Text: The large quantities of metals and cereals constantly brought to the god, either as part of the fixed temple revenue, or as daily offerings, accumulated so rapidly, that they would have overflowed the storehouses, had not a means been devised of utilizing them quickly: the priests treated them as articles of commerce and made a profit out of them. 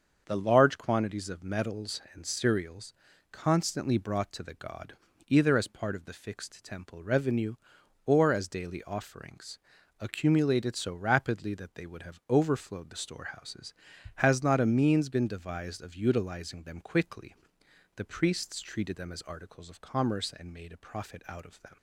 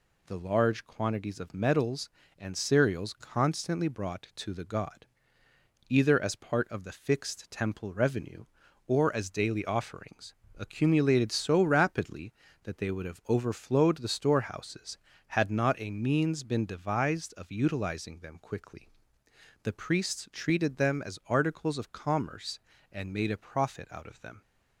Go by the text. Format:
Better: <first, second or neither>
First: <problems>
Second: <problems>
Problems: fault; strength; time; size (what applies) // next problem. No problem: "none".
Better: second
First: starts louder than the rest; until 1.2 s; 7 dB // pauses between "cereals" and "constantly"; slight; at 2.9 s; 0.36 s long // says "has" for "had"; at 14.1 s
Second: none